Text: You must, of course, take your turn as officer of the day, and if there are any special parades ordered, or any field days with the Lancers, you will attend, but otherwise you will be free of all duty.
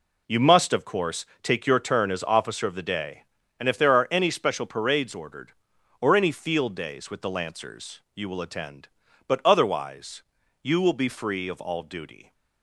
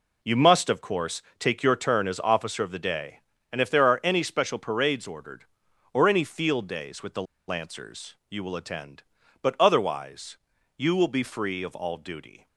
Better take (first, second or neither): first